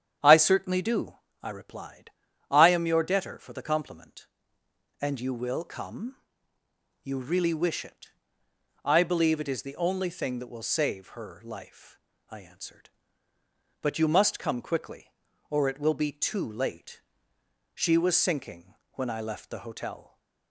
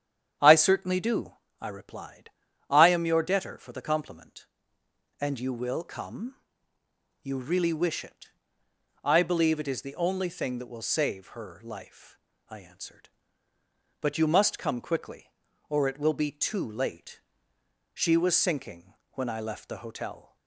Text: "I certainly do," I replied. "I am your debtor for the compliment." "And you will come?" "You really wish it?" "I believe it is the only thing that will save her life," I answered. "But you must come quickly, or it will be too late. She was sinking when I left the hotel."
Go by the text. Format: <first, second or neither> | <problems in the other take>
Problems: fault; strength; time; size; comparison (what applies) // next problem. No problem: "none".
neither | starts louder than the rest; strong; the same in both // pauses between "sinking" and "when"; slight; the same in both